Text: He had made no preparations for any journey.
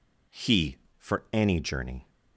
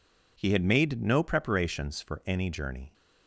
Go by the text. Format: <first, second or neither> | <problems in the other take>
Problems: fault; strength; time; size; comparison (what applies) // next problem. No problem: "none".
second | skips "had made no preparations"; at 0.8 s